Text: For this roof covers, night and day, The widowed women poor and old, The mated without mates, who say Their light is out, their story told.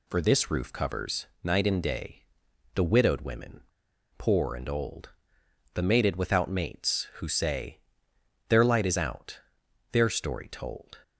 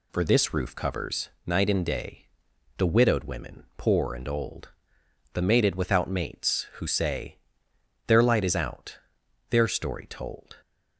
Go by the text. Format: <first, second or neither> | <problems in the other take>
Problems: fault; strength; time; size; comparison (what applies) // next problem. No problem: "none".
second | pauses between "women" and "poor"; noticeable; at 3.6 s; 0.53 s long // pauses between "say" and "Their"; noticeable; at 7.8 s; 0.68 s long; noticeable in the second